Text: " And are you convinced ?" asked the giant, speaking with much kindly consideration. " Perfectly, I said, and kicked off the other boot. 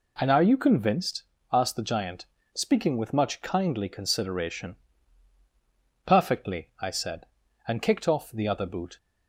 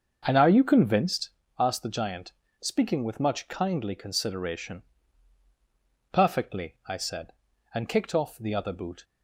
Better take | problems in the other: first | starts louder than the rest; strong; until 1.4 s; 7.5 dB

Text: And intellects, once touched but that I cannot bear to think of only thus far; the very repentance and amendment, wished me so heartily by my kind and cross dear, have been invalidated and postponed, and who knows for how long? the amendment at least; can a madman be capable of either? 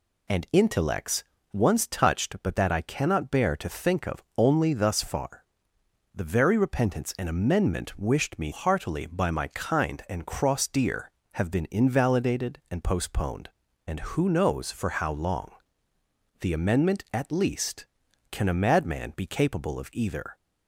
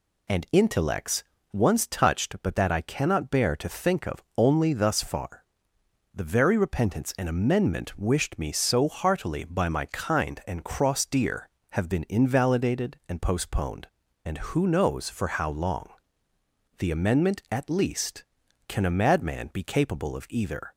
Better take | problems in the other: second | pauses between "of" and "only"; slight; at 4.2 s; 0.16 s long; slight in the second // skips "so"; at 8.5 s

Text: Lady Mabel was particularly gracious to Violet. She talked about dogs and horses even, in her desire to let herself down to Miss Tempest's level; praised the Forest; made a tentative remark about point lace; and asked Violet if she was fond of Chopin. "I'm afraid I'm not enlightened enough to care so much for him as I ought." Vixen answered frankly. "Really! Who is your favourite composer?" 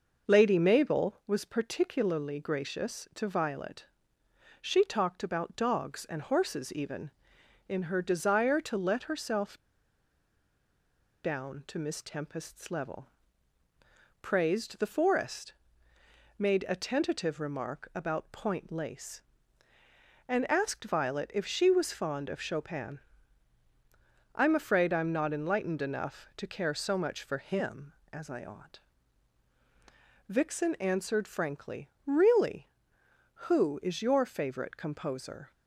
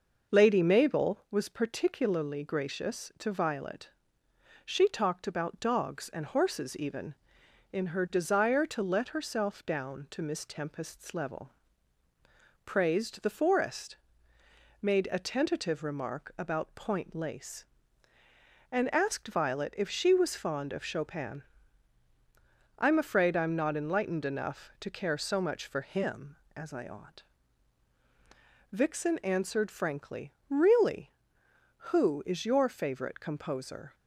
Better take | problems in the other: second | pauses between "herself" and "down"; strong; at 9.5 s; 1.6 s long

